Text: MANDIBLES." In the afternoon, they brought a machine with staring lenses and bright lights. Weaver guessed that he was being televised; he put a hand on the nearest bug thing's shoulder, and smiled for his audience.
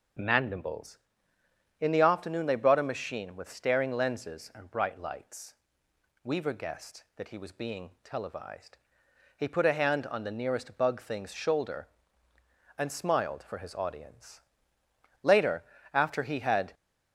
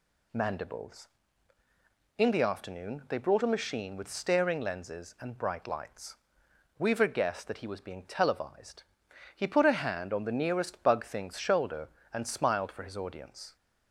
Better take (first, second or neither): second